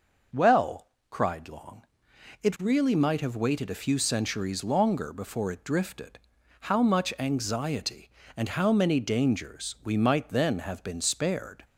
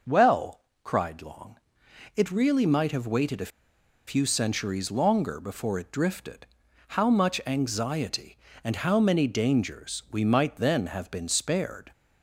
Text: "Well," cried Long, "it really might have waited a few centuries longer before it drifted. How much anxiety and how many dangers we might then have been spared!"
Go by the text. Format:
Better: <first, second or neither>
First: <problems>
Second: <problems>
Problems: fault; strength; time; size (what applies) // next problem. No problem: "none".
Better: first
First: none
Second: pauses between "a" and "few"; noticeable; at 3.5 s; 0.58 s long